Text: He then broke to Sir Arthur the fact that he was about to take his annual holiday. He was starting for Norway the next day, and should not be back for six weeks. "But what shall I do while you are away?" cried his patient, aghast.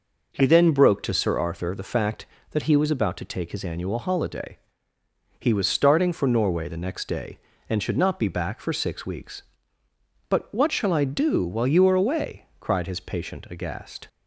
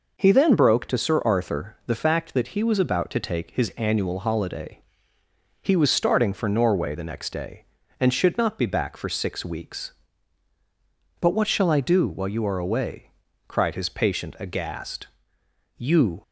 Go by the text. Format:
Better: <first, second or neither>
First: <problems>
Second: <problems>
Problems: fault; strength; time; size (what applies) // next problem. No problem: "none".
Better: first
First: none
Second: goes on to say "You"; slight; from 15.7 s on; 0.46 s long